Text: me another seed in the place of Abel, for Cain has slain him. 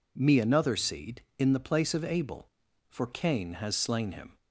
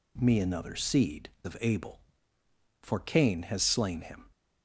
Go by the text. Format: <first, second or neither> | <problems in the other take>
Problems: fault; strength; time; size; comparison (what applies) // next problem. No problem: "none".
first | skips "in the place"; at 1.3 s